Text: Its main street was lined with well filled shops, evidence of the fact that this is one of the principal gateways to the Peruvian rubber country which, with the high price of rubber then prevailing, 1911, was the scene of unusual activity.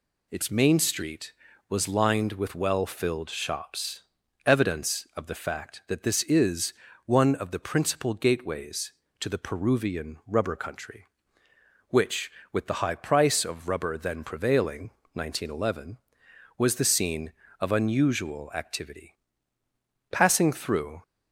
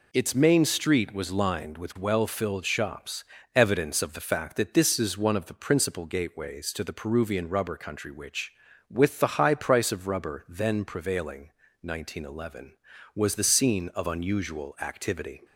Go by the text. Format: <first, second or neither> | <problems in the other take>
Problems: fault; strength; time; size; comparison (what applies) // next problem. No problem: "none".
second | pauses between "is" and "one"; slight; at 6.7 s; 0.32 s long // goes on to say "Passing through"; noticeable; from 20.1 s on; 0.92 s long